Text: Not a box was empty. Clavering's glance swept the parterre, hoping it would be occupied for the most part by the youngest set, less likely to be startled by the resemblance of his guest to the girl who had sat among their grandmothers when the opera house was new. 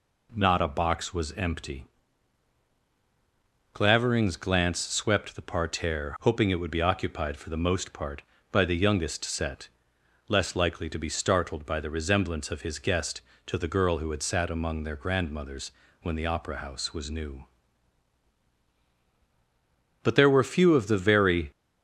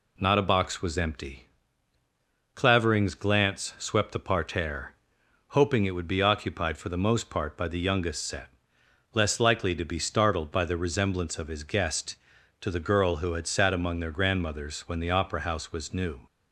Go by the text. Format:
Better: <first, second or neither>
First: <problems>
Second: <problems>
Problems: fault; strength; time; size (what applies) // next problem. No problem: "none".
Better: second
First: pauses between "grandmothers" and "when"; slight; at 15.7 s; 0.30 s long // goes on to say "But there were few of the very"; from 20.0 s on; 1.4 s long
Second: none